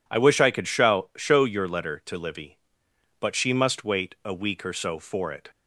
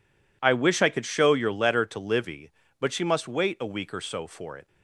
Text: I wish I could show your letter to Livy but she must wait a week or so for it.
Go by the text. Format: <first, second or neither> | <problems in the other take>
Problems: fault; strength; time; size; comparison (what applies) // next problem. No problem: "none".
second | says "show" twice; at 1.1 s